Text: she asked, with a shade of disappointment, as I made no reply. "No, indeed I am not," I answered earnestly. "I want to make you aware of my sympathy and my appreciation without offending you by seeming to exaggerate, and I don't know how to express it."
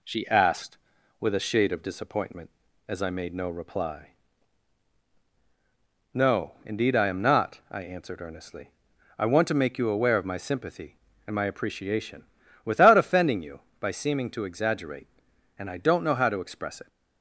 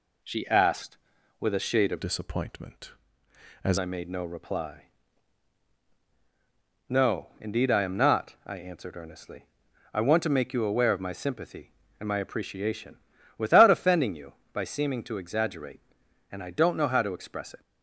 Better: first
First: pauses between "appreciation" and "without"; at 12.2 s; 0.40 s long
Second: changes voice from "disappointment" to "as"; from 2.0 to 3.7 s; 1.7 s long // pauses between "appreciation" and "without"; at 12.9 s; 0.40 s long

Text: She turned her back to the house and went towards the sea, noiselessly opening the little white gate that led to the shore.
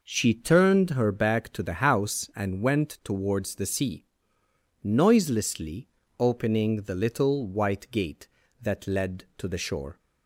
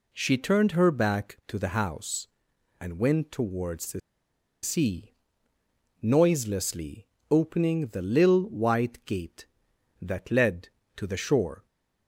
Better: first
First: pauses between "noiselessly" and "opening"; slight; at 5.8 s; 0.32 s long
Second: pauses between "the" and "sea"; noticeable; at 4.0 s; 0.63 s long // pauses between "noiselessly" and "opening"; slight; at 7.0 s; 0.26 s long

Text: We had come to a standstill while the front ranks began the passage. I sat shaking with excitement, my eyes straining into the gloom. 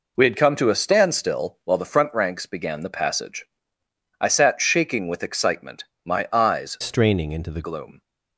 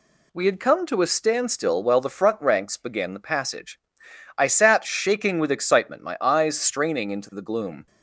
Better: second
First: changes voice from "straining" to "the"; from 6.8 to 7.6 s; 0.8 s long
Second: none

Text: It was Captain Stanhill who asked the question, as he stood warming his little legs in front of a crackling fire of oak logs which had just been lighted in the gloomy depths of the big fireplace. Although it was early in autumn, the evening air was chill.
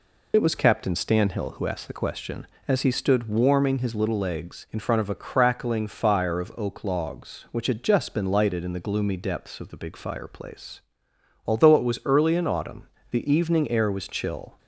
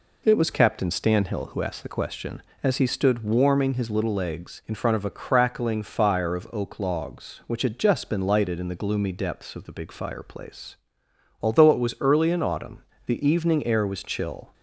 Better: second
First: loses the start of "It"; at 0.3 s; 45 ms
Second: none

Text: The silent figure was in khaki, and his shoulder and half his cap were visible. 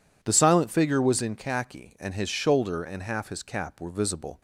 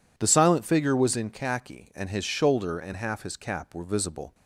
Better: neither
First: none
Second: none

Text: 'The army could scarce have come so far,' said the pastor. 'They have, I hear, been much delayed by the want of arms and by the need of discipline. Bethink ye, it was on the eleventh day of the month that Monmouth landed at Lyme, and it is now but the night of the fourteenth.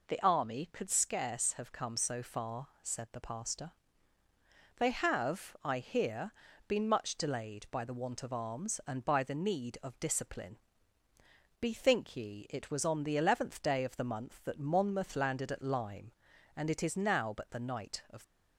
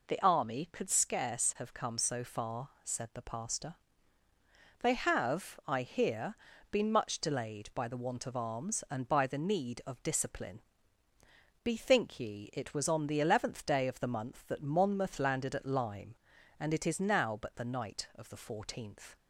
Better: second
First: stops before "the fourteenth"; at 18.2 s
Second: none

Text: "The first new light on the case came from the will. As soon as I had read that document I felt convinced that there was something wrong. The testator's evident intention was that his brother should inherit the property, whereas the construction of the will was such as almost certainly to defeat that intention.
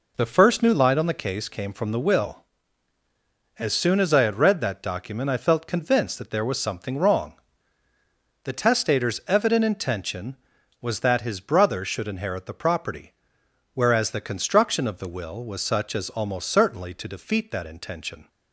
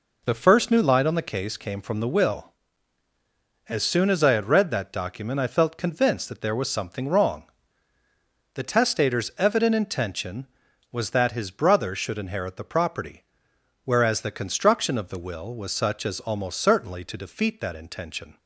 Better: neither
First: none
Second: none

